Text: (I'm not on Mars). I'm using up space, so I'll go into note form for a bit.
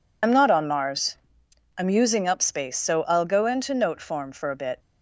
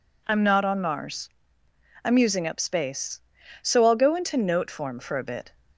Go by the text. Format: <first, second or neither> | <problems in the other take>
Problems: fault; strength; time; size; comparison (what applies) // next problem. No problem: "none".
second | loses the start of "I'm"; at 0.2 s; 60 ms